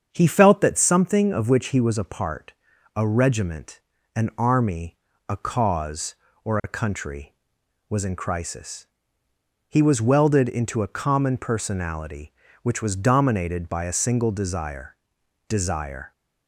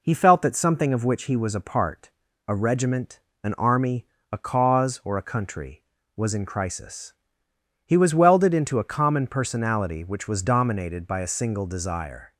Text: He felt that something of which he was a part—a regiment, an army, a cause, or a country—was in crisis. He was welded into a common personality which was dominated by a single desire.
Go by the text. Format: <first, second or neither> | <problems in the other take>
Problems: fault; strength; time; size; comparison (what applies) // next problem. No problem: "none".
second | starts louder than the rest; strong; until 1.1 s; 7.5 dB // says "desire" twice; at 15.4 s